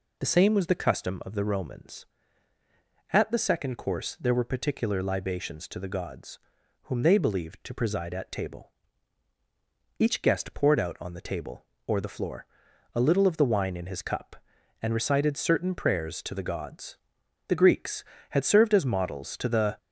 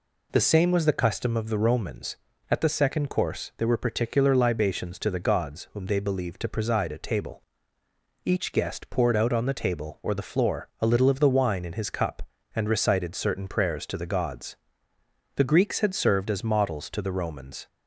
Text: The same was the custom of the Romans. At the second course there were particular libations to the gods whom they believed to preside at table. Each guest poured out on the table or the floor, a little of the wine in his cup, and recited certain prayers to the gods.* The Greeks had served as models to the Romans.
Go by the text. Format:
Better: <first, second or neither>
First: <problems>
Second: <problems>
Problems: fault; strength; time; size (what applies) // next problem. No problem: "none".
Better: second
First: pauses between "gods" and "whom"; at 6.3 s; 0.44 s long // stops before "Romans"; at 19.7 s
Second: none